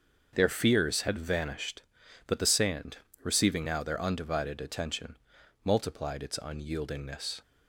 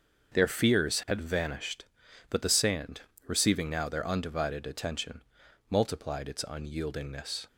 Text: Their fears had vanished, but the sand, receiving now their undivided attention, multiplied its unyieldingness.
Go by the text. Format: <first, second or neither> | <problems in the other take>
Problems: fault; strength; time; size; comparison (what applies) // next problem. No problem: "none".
neither | starts louder than the rest; the same in both